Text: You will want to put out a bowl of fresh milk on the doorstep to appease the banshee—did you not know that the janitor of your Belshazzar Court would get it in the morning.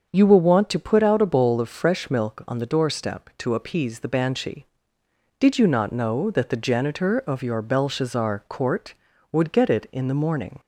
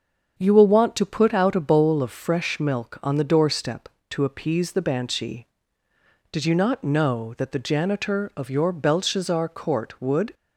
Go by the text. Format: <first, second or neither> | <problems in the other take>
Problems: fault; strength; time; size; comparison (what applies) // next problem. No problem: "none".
first | starts louder than the rest; until 1.4 s; 7 dB; also in the first // stops before "get it in the morning"; at 10.3 s